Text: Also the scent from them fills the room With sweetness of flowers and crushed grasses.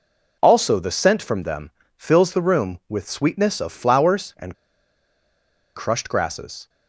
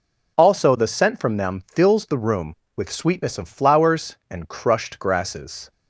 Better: second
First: pauses between "them" and "fills"; slight; at 1.7 s; 0.24 s long // pauses between "and" and "crushed"; at 4.5 s; 1.2 s long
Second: none

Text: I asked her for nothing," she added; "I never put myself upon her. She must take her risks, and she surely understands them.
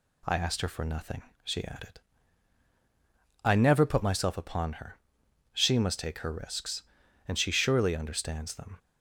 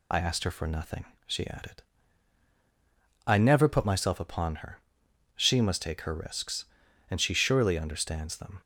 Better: first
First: none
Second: loses the start of "I"; at 0.1 s; 50 ms

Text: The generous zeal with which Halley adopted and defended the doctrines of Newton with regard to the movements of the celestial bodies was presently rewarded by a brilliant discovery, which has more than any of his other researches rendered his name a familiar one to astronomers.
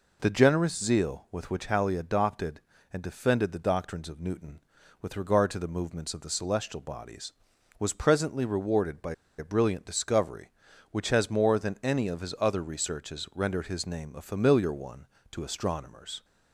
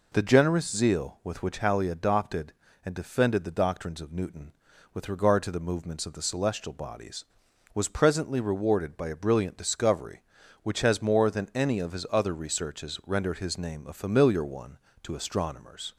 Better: second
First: pauses between "by" and "a"; slight; at 9.1 s; 0.23 s long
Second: none

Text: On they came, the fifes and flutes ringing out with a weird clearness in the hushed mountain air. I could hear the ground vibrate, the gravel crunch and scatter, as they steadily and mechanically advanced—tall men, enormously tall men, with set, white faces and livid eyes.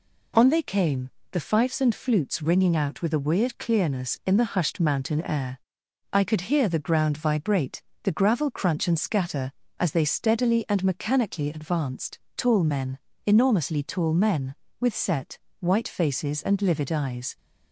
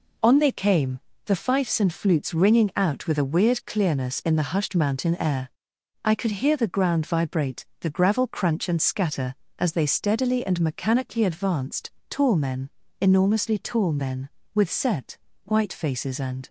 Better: first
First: none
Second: stops before "livid eyes"; at 16.4 s

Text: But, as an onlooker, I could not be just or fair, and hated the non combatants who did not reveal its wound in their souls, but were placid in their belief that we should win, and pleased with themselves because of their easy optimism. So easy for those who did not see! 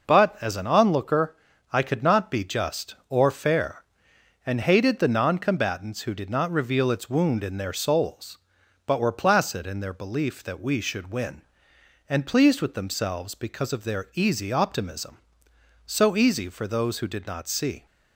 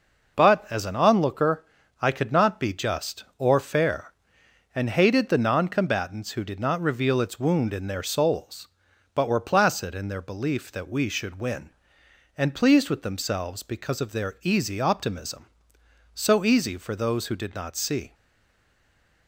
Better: first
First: none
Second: stays silent after the last word; noticeable; from 18.1 s on; 1.1 s long

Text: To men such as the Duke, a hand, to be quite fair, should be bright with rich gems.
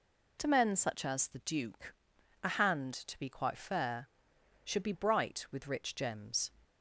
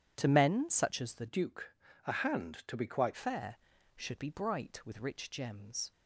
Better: first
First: none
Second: changes voice from "Duke" to "quite"; from 1.2 to 3.1 s; 1.9 s long

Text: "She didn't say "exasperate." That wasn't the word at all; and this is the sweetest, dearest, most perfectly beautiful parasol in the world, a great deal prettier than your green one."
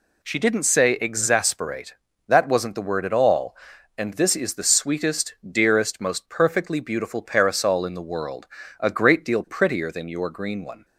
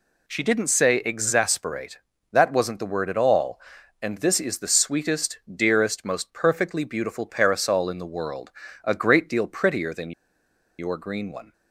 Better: first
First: none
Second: pauses between "than" and "your"; noticeable; at 10.1 s; 0.67 s long

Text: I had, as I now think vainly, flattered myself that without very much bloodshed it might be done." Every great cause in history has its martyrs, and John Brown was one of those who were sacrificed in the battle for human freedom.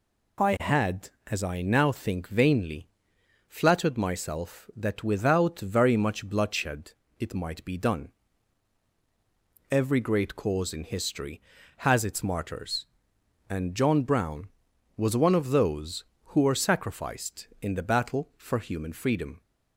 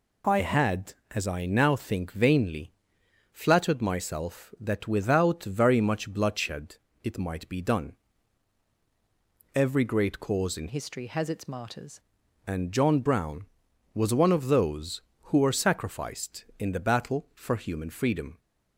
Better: first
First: pauses between "bloodshed" and "it"; slight; at 6.9 s; 0.28 s long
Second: pauses between "bloodshed" and "it"; slight; at 6.7 s; 0.28 s long // changes voice from "history" to "martyrs"; from 10.6 to 12.0 s; 1.4 s long

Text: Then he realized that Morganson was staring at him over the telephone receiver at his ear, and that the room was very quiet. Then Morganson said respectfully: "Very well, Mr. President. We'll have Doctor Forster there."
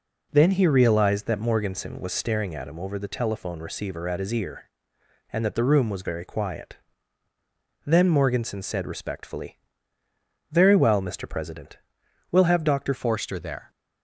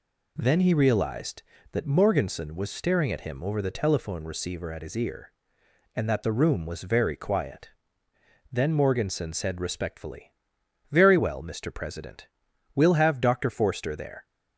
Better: second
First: changes voice at "Forster"; from 12.9 s on; 0.7 s long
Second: none

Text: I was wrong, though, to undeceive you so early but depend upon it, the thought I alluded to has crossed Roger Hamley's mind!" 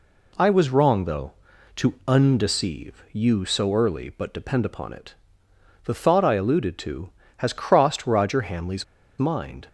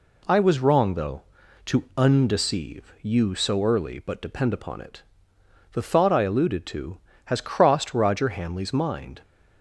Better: second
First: pauses between "Hamley's" and "mind"; slight; at 8.8 s; 0.35 s long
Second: none

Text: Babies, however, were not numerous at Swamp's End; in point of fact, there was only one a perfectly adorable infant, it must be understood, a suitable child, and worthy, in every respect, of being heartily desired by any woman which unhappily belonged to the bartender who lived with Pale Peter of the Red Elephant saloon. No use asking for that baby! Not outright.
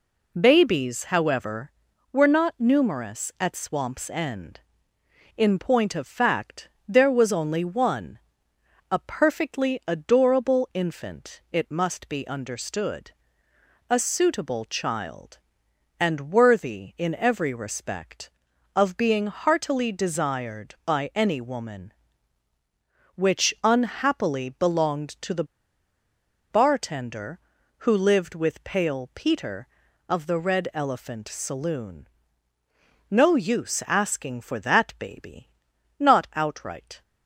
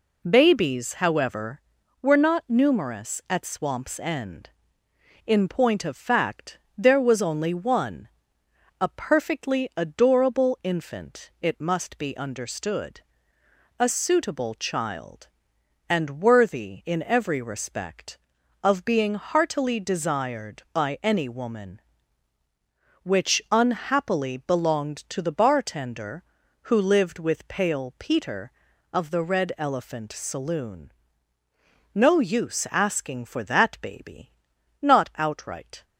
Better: second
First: pauses between "one" and "a"; noticeable; at 8.1 s; 0.72 s long // pauses between "the" and "bartender"; at 25.4 s; 1.0 s long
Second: pauses between "one" and "a"; noticeable; at 8.0 s; 0.72 s long

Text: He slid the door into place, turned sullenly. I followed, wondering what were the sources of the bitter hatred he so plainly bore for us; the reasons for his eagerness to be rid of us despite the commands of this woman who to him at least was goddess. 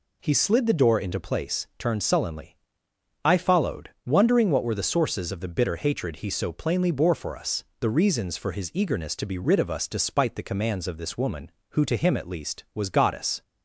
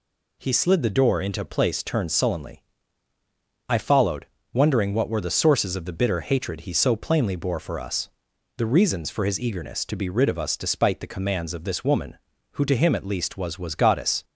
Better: first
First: none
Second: says "was" twice; at 13.5 s

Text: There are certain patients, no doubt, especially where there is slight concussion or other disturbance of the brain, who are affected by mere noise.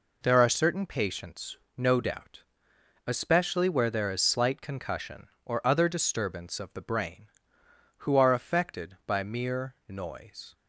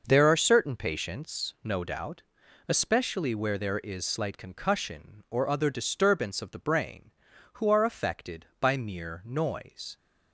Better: neither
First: none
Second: none

